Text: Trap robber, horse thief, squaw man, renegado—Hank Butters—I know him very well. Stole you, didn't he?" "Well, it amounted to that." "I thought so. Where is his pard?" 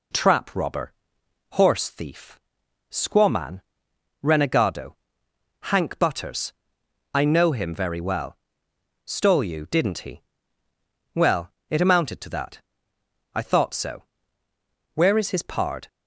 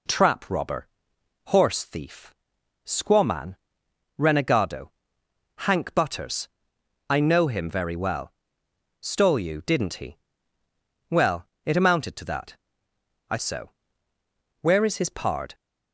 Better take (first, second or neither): first